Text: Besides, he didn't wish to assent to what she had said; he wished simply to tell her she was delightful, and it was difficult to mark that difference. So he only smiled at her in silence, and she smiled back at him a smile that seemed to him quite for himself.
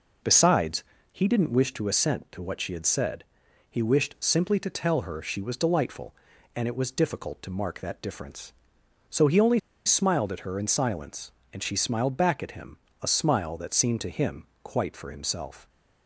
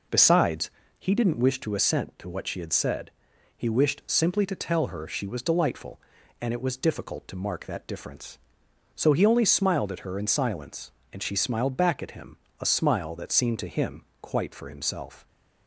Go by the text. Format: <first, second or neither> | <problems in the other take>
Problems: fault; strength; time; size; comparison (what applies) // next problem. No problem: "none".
second | pauses between "only" and "smiled"; slight; at 9.5 s; 0.26 s long // pauses between "him" and "a"; slight; at 12.7 s; 0.24 s long; slight in the second // pauses between "him" and "quite"; slight; at 14.4 s; 0.16 s long; slight in the second